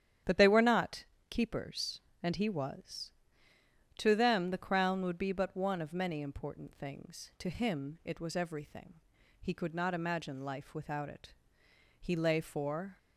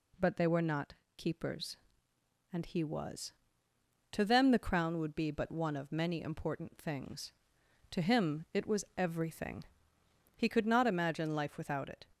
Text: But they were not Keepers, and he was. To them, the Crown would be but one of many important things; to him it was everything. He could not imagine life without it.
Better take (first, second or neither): second